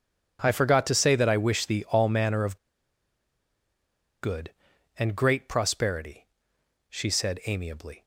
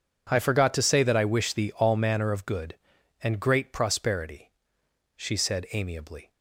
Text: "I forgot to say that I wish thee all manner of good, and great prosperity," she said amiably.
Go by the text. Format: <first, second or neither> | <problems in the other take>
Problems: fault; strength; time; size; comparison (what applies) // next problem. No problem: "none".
second | pauses between "of" and "good"; strong; at 2.5 s; 1.6 s long